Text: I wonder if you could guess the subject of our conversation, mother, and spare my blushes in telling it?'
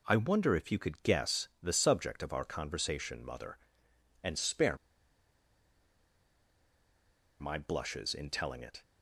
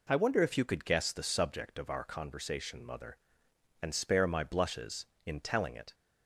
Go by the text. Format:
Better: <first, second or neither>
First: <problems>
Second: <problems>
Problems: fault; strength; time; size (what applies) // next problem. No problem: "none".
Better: second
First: pauses between "spare" and "my"; strong; at 4.7 s; 2.6 s long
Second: none